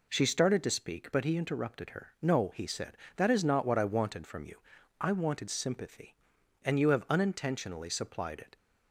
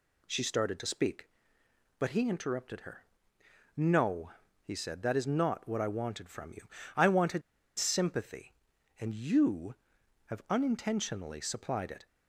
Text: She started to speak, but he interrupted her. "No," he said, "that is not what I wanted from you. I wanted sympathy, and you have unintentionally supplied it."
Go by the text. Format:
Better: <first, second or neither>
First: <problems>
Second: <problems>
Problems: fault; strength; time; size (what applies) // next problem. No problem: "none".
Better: first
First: none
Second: pauses between "wanted" and "sympathy"; at 7.4 s; 0.36 s long